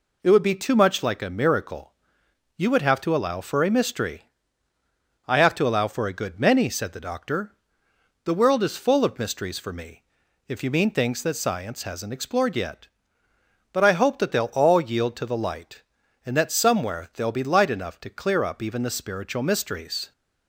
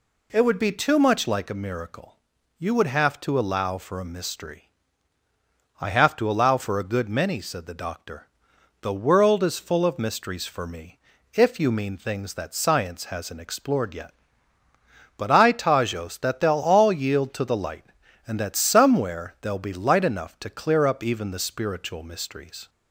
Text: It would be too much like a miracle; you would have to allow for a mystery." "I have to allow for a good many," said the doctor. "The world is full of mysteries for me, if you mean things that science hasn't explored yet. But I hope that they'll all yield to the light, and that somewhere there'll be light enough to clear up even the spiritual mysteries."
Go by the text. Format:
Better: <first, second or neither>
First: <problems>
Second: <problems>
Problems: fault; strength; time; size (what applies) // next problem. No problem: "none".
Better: first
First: none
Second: says "tajos" for "hope"; at 15.5 s